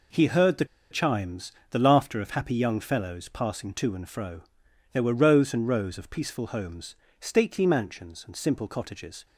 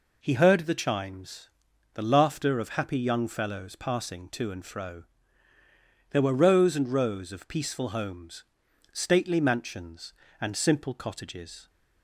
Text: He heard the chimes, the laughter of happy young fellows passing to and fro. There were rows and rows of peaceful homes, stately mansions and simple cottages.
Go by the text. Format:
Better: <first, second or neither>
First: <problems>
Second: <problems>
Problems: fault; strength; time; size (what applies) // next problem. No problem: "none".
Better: second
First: pauses between "the" and "chimes"; slight; at 0.6 s; 0.25 s long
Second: none